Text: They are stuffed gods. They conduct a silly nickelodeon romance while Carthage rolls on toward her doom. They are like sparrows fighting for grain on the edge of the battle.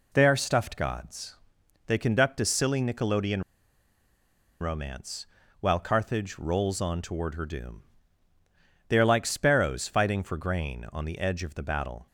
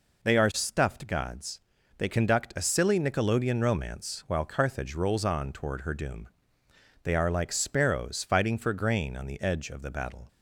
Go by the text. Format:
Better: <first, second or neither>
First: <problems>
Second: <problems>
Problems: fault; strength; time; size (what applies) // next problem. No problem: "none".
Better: second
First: pauses between "nickelodeon" and "romance"; at 3.4 s; 1.1 s long // pauses between "romance" and "while"; slight; at 5.2 s; 0.34 s long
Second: none